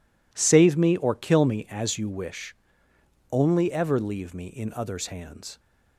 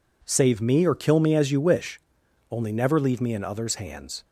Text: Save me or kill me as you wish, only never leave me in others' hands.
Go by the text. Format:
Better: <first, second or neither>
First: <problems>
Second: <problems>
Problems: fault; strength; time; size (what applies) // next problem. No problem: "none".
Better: second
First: says "ever" for "never"; at 3.6 s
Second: none